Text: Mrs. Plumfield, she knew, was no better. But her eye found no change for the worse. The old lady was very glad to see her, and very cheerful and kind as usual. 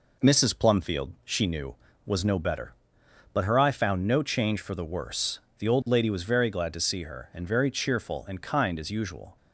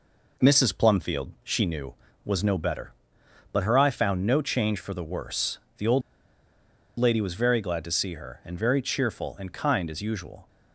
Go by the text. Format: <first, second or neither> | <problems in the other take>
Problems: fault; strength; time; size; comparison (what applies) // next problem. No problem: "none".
first | pauses between "old" and "lady"; noticeable; at 6.0 s; 0.98 s long